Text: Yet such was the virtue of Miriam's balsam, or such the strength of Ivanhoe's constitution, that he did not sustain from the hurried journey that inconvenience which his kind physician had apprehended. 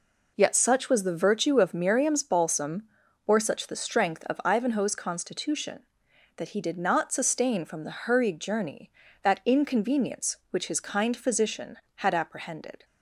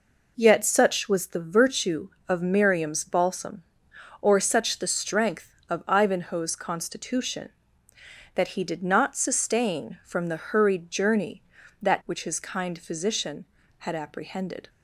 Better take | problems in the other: first | skips "inconvenience"; at 12.0 s

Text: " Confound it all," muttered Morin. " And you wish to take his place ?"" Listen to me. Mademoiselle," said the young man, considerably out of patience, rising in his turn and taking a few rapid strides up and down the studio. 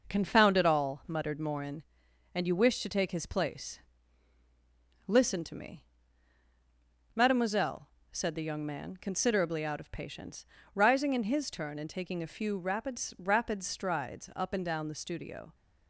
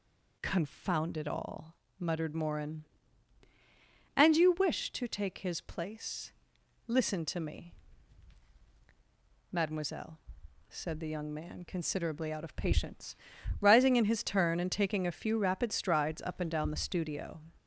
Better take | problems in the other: second | says "rapid" twice; at 13.1 s

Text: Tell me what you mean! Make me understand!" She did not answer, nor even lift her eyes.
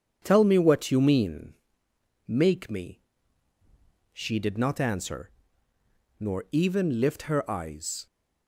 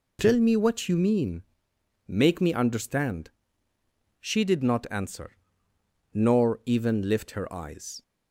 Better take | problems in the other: second | skips "understand"; at 3.5 s

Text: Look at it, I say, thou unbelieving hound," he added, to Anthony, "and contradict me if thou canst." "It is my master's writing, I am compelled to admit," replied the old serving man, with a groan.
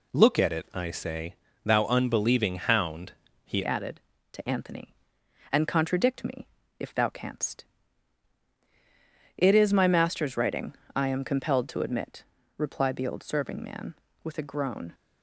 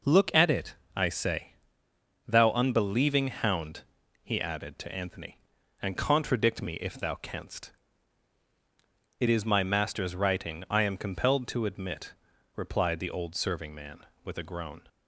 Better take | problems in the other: second | changes voice at "added"; from 3.6 s on; 11.3 s long // pauses between "me" and "if"; slight; at 6.4 s; 0.32 s long

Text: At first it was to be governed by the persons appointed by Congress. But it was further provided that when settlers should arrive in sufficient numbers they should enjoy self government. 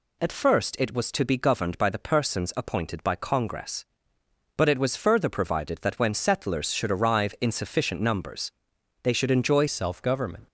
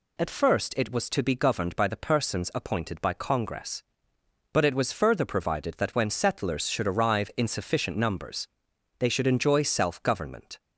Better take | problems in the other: second | pauses between "numbers" and "they"; noticeable; at 8.5 s; 0.52 s long; noticeable in the second // changes voice at "self"; from 9.6 s on; 0.8 s long

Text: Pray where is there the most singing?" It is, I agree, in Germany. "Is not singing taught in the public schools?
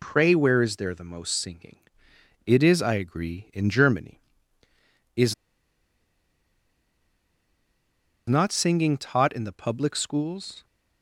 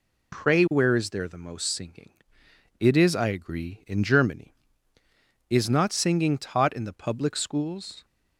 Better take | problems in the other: second | pauses between "Is" and "not"; strong; at 5.3 s; 2.9 s long

